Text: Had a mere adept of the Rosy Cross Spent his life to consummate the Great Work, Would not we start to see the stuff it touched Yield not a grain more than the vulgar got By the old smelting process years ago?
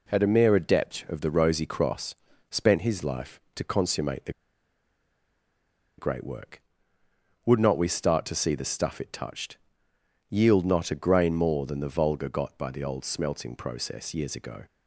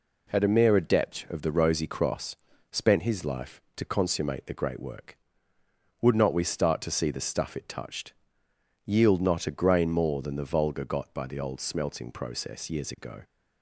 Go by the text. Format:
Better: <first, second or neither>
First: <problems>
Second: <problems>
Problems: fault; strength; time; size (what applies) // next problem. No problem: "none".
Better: second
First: pauses between "Cross" and "Spent"; slight; at 2.1 s; 0.34 s long // pauses between "the" and "Great"; strong; at 4.3 s; 1.6 s long // pauses between "touched" and "Yield"; noticeable; at 9.5 s; 0.72 s long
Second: pauses between "Cross" and "Spent"; slight; at 2.3 s; 0.34 s long // pauses between "touched" and "Yield"; noticeable; at 8.1 s; 0.72 s long